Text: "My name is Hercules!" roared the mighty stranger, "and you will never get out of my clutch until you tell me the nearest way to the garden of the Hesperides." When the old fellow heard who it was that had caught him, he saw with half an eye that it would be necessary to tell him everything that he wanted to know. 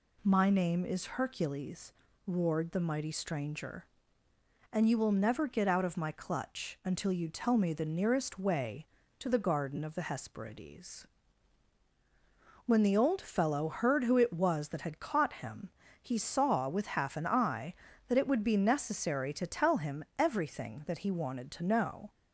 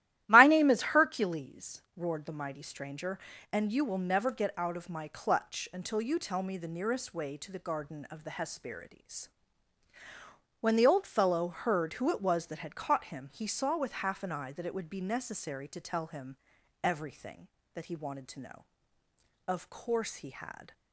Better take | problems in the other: first | starts louder than the rest; strong; until 1.2 s; 14 dB // pauses between "him" and "everything"; noticeable; at 16.3 s; 0.46 s long // goes on to say "Of course he had"; noticeable; from 19.4 s on; 1.2 s long

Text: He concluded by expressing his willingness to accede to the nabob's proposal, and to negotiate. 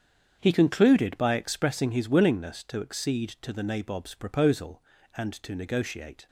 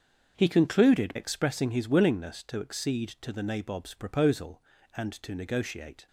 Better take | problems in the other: first | starts louder than the rest; until 1.3 s; 7 dB; strong in the first // skips "by"; at 1.1 s

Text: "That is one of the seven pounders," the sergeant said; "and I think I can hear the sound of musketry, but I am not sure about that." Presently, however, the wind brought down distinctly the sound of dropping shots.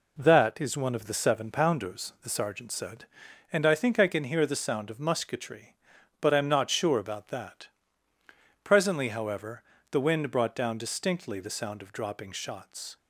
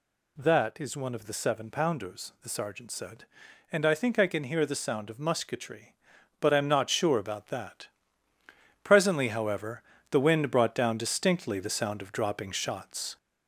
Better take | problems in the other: first | gets louder; noticeable; throughout; 4 dB

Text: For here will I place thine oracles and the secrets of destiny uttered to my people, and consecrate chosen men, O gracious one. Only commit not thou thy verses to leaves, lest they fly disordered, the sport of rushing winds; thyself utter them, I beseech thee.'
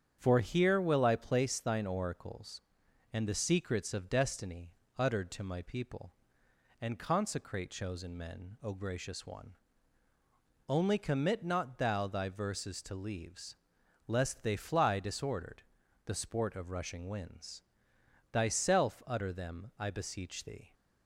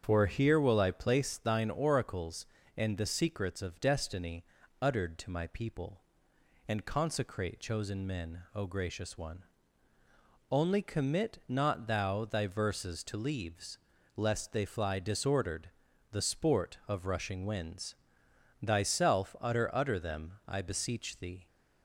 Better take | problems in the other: first | starts louder than the rest; strong; until 1.0 s; 7.5 dB; strong in the first // pauses between "destiny" and "uttered"; slight; at 4.4 s; 0.34 s long; slight in the first // says "utter" twice; at 19.7 s

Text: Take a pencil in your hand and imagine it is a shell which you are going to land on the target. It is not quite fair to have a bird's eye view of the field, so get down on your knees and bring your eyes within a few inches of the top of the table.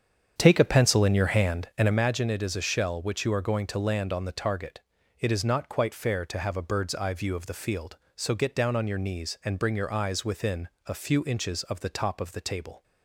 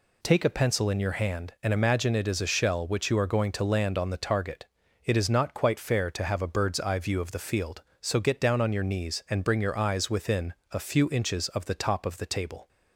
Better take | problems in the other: second | starts louder than the rest; strong; until 2.0 s; 8 dB // pauses between "within" and "a"; slight; at 10.6 s; 0.16 s long; slight in the second

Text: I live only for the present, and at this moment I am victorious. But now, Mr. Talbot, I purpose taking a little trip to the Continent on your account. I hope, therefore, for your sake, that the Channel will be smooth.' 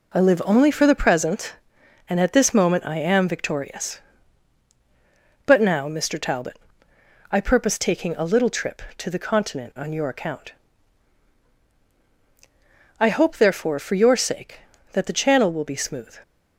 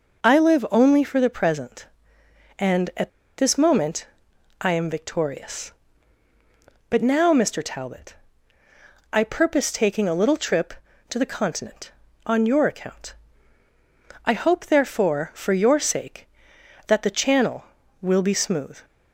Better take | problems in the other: first | pauses between "at" and "this"; slight; at 3.0 s; 0.29 s long // pauses between "moment" and "I"; noticeable; at 4.0 s; 0.56 s long

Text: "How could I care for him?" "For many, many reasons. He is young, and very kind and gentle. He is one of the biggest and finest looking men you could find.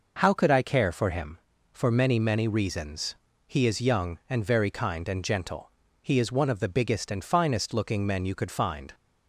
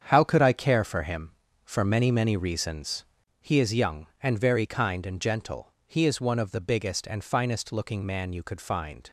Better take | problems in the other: first | starts louder than the rest; strong; until 1.0 s; 7.5 dB // says "man" for "men"; at 8.0 s

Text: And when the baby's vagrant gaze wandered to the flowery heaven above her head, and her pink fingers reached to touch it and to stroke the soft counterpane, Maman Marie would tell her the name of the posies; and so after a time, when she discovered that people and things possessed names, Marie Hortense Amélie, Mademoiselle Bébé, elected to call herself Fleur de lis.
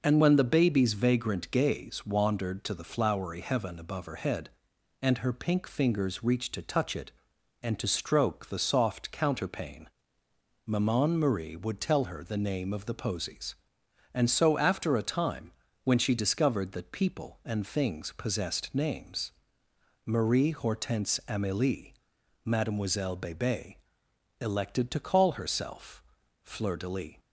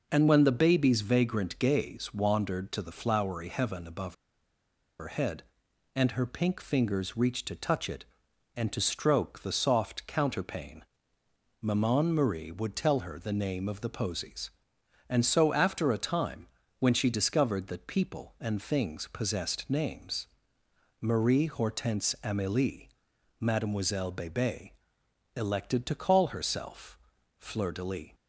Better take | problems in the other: first | pauses between "above" and "her"; noticeable; at 4.1 s; 0.86 s long // pauses between "herself" and "Fleur"; at 26.9 s; 0.42 s long; also in the first

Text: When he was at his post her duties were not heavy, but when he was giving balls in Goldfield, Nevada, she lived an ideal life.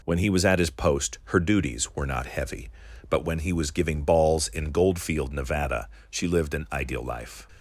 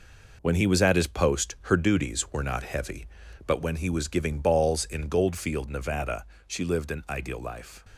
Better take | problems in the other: first | gets quieter; throughout; 6.5 dB

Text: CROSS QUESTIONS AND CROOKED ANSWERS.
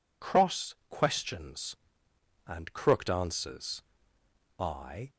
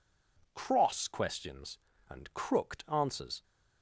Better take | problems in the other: second | goes on to say "I"; from 4.5 s on; 0.52 s long

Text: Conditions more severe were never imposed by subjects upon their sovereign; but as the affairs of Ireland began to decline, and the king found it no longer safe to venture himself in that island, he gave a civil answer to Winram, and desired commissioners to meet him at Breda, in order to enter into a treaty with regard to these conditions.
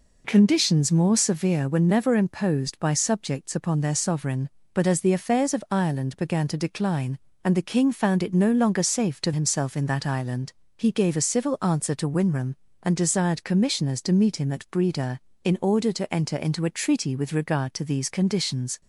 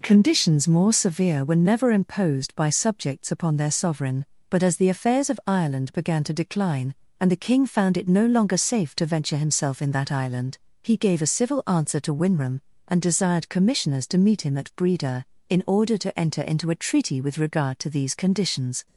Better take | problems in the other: second | skips "venture"; at 9.3 s

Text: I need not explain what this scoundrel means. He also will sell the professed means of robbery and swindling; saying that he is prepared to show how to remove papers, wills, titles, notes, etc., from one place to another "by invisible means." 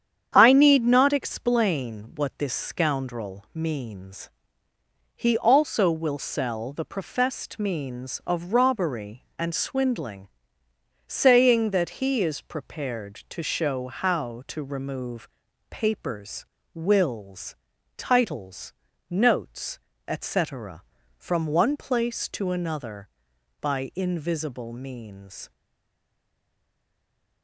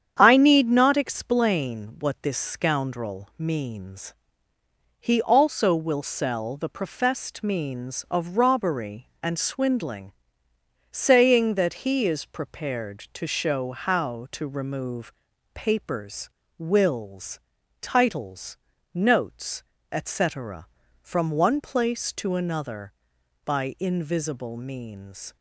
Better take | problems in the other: second | starts louder than the rest; strong; until 1.3 s; 8.5 dB; strong in the second // pauses between "remove" and "papers"; at 15.2 s; 0.42 s long; also in the second // stays silent after the last word; noticeable; from 25.5 s on; 1.9 s long

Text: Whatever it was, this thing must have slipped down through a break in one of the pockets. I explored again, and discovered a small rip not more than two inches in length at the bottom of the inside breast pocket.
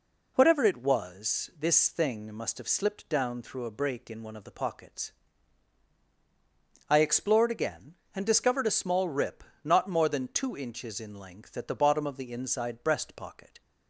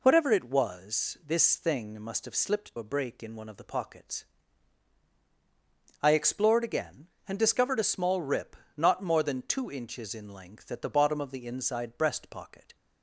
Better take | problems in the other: first | skips "down through"; at 2.7 s // pauses between "rip" and "not"; slight; at 8.5 s; 0.22 s long; slight in the first

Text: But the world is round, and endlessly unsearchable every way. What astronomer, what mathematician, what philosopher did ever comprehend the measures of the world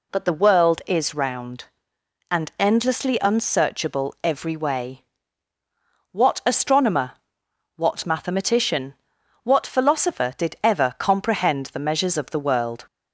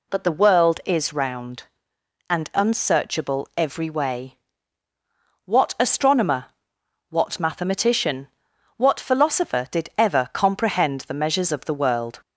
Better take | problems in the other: first | skips "endlessly"; at 2.5 s

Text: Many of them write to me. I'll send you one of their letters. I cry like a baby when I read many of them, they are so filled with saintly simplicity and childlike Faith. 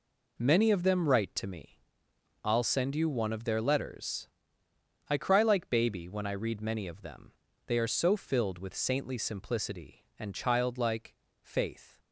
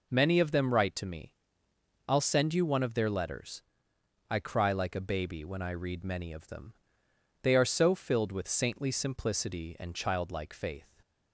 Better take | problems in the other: second | skips "a"; at 5.6 s // pauses between "childlike" and "Faith"; slight; at 11.1 s; 0.30 s long

